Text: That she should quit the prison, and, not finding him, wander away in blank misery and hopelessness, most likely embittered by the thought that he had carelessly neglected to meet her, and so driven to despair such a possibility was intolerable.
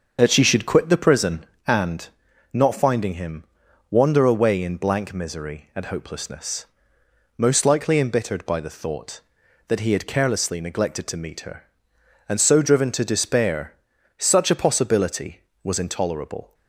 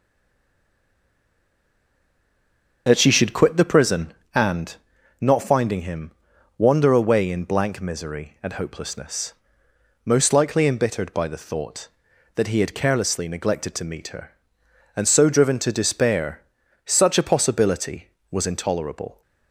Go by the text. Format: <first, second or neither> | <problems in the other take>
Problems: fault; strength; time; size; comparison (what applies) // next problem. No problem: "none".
first | stays silent before the first word; strong; until 2.8 s; 2.8 s long // starts louder than the rest; until 3.8 s; 6.5 dB; also in the first // pauses between "despair" and "such"; at 16.4 s; 0.44 s long; also in the first